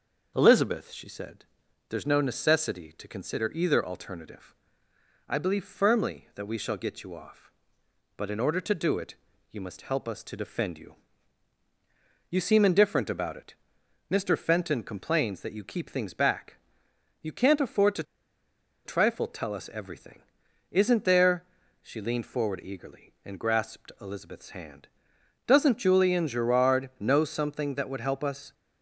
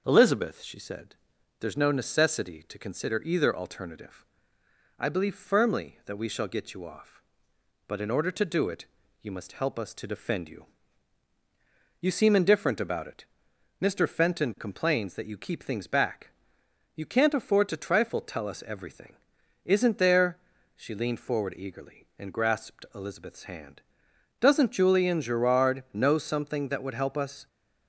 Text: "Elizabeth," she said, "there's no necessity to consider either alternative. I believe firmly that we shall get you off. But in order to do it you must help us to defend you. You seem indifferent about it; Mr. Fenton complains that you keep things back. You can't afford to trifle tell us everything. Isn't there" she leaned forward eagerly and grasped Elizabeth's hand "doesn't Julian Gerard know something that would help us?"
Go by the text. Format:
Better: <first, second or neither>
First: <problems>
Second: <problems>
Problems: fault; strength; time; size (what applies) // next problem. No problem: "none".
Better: second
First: starts louder than the rest; noticeable; until 1.3 s; 6 dB // pauses between "it" and "you"; slight; at 9.1 s; 0.36 s long // pauses between "to" and "trifle"; noticeable; at 18.0 s; 0.81 s long // pauses between "there" and "she"; at 21.4 s; 0.38 s long // pauses between "hand" and "doesn't"; noticeable; at 24.8 s; 0.58 s long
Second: starts louder than the rest; noticeable; until 1.0 s; 6 dB // pauses between "it" and "you"; slight; at 8.8 s; 0.36 s long // pauses between "there" and "she"; at 20.3 s; 0.38 s long // pauses between "hand" and "doesn't"; noticeable; at 23.8 s; 0.58 s long